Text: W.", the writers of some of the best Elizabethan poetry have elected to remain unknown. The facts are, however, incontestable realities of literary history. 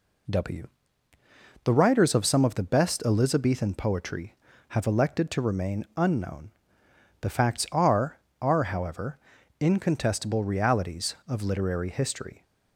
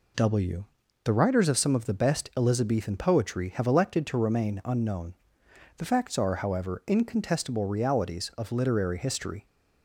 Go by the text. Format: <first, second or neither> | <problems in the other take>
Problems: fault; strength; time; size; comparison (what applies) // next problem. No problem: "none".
second | says "are" twice; at 8.4 s